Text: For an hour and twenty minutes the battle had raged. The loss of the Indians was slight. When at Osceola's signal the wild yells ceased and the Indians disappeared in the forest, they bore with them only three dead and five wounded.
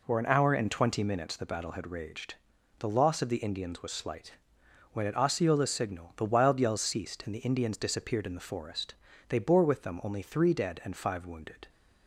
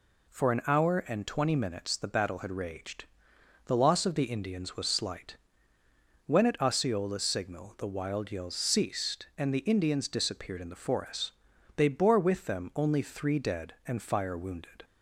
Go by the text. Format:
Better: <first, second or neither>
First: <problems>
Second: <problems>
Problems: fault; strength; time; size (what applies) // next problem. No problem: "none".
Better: first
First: none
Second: says "fire" for "five"; at 14.0 s